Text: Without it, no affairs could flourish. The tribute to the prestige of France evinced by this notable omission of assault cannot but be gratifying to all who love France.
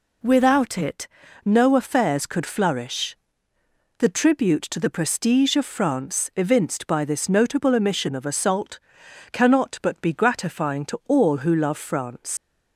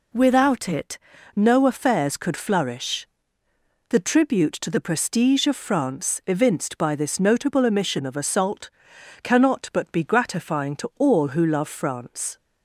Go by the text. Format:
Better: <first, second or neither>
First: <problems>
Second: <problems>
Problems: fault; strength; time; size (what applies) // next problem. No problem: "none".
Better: second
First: pauses between "assault" and "cannot"; noticeable; at 8.7 s; 0.54 s long // leaves "France" unfinished; at 12.3 s; 90 ms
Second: pauses between "assault" and "cannot"; noticeable; at 8.6 s; 0.54 s long